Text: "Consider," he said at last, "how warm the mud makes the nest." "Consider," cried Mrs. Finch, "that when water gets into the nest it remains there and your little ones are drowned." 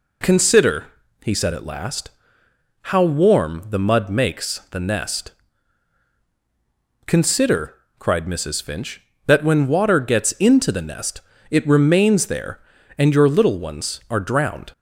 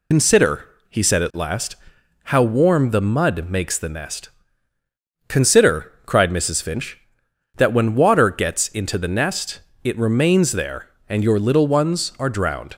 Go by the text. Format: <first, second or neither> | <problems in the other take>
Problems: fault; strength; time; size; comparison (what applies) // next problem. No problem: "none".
first | loses the start of "Consider"; at 0.1 s; 70 ms // pauses between "nest" and "it"; slight; at 9.6 s; 0.22 s long; slight in the first